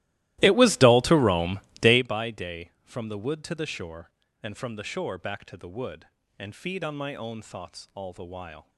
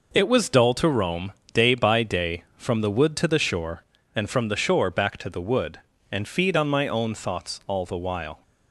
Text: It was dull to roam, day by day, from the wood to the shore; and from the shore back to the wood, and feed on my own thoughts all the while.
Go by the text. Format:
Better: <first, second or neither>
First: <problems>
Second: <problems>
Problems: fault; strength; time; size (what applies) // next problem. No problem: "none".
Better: second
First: starts louder than the rest; strong; until 2.1 s; 17 dB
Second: none